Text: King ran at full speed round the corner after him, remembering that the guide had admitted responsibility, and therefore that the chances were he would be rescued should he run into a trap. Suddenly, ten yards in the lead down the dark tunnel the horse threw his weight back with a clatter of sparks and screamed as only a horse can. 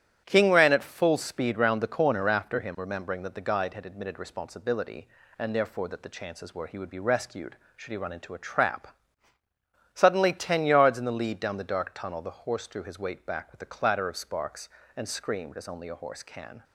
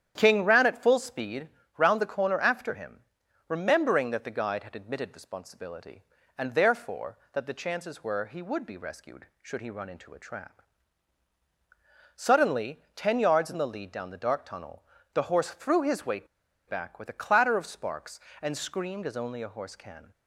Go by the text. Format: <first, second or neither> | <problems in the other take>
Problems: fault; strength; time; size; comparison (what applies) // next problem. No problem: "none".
first | starts louder than the rest; strong; until 1.1 s; 10 dB; strong in the first // pauses between "speed" and "round"; slight; at 1.4 s; 0.28 s long // pauses between "tunnel" and "the"; slight; at 14.8 s; 0.30 s long // pauses between "weight" and "back"; at 16.2 s; 0.41 s long